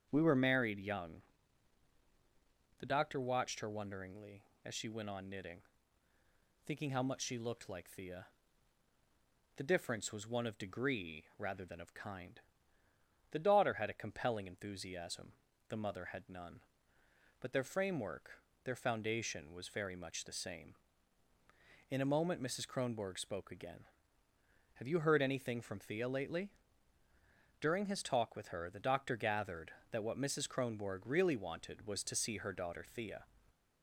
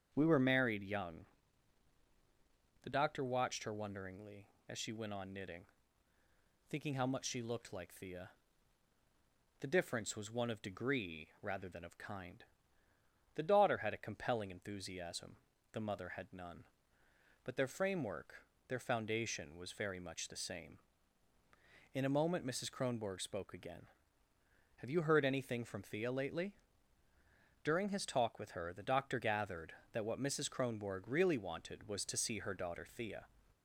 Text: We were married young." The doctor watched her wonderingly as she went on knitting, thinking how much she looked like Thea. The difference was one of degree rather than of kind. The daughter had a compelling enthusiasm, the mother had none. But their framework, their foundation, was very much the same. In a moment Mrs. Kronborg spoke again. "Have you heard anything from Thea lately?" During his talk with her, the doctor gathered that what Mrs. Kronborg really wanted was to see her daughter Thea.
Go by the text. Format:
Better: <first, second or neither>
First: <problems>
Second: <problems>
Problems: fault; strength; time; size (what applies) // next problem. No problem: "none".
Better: neither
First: starts louder than the rest; strong; until 1.1 s; 7.5 dB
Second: starts louder than the rest; strong; until 1.1 s; 7.5 dB